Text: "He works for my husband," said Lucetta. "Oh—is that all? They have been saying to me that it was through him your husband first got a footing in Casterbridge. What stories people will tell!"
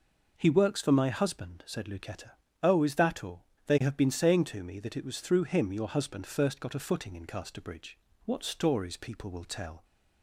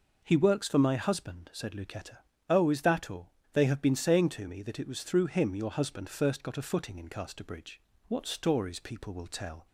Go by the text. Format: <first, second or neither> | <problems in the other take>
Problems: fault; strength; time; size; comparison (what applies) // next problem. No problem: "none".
neither | none